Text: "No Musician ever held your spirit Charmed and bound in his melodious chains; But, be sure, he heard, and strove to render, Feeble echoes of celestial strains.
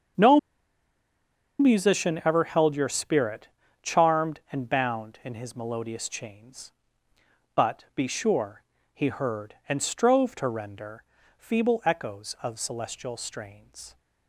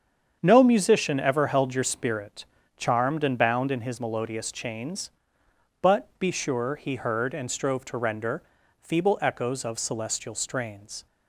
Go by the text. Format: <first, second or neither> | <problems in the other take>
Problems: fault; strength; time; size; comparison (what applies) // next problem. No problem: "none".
second | starts louder than the rest; strong; until 2.4 s; 8 dB; strong in the second // pauses between "No" and "Musician"; at 0.3 s; 1.2 s long // pauses between "spirit" and "Charmed"; slight; at 3.4 s; 0.34 s long; slight in the second